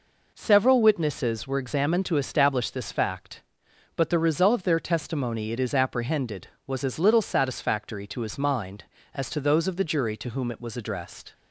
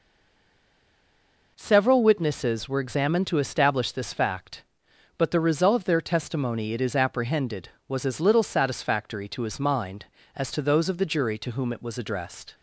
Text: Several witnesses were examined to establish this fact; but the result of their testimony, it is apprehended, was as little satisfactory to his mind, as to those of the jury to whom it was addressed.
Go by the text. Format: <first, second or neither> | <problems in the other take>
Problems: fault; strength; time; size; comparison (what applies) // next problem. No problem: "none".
first | stays silent before the first word; noticeable; until 1.5 s; 1.5 s long